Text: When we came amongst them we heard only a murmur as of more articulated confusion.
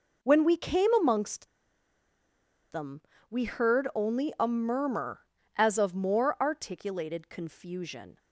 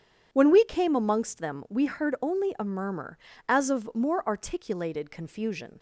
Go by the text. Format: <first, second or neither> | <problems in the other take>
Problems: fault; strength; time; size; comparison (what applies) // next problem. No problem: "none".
second | pauses between "amongst" and "them"; at 1.4 s; 1.2 s long // pauses between "them" and "we"; slight; at 3.0 s; 0.28 s long